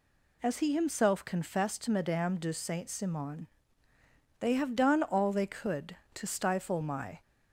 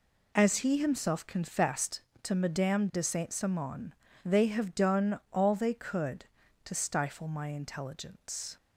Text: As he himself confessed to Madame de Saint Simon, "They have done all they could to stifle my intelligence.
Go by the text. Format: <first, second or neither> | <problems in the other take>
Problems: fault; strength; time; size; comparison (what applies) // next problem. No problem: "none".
second | stops before "intelligence"; at 7.2 s